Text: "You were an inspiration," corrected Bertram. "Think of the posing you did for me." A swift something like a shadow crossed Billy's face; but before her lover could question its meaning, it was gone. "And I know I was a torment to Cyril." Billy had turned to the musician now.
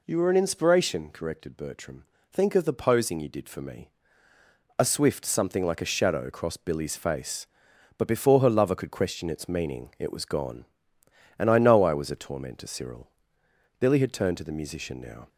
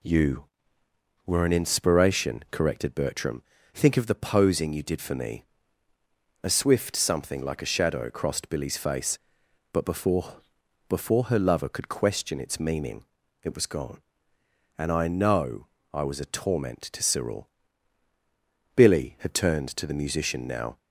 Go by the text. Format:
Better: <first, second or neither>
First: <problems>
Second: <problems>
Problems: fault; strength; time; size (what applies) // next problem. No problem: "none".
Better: first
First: none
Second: says "before" twice; at 10.8 s // pauses between "know" and "I"; slight; at 15.6 s; 0.26 s long